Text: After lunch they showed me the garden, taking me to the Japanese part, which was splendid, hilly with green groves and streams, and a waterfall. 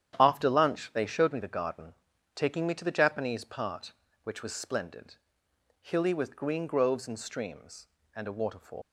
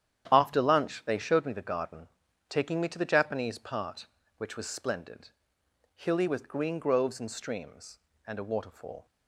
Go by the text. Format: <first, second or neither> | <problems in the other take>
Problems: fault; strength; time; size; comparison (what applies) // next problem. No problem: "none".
second | starts louder than the rest; strong; until 1.2 s; 10 dB; strong in the second // leaves "waterfall" unfinished; at 8.8 s; 125 ms